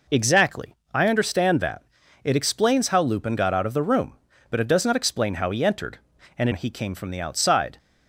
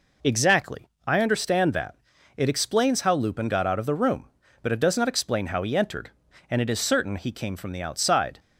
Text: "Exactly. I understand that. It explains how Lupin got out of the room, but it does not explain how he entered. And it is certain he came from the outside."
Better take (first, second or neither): second